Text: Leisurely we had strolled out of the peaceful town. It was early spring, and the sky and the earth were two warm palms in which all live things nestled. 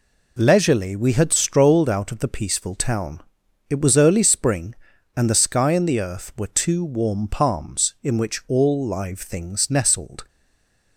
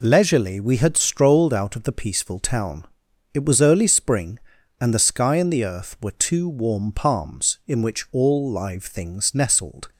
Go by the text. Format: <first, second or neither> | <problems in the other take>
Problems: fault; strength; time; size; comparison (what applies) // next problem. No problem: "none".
second | stays silent after the last word; slight; from 10.2 s on; 0.7 s long